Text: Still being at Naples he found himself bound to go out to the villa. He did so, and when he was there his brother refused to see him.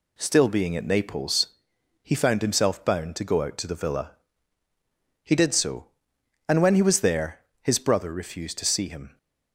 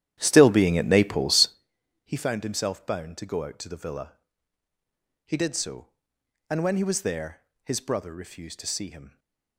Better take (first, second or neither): first